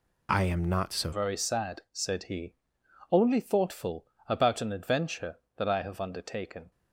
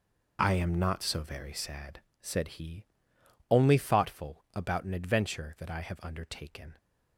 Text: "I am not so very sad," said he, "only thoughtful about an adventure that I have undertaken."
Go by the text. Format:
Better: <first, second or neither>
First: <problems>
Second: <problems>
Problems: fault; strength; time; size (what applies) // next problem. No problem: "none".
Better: second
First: changes voice at "very"; from 1.1 s on; 5.6 s long // pauses between "thoughtful" and "about"; slight; at 4.0 s; 0.22 s long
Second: none